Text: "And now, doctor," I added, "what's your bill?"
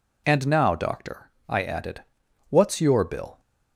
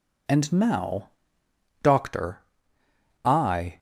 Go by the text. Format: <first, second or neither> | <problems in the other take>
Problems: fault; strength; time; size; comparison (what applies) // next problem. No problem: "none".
first | stops before "added what's your bill"; at 3.7 s